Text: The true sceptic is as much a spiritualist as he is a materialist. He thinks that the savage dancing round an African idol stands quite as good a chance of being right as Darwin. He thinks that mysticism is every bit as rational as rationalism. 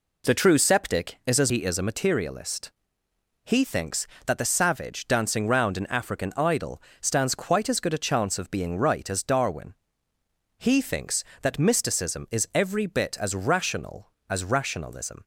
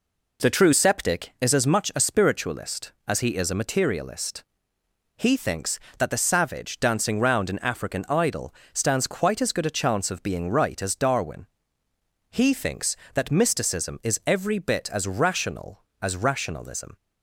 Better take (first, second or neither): second